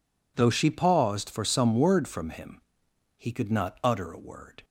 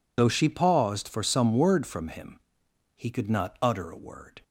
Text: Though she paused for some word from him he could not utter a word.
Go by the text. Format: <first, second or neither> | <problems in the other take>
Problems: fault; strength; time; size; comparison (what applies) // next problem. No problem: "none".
first | loses the start of "Though"; at 0.1 s; 35 ms // pauses between "him" and "he"; noticeable; at 2.3 s; 0.58 s long; noticeable in the first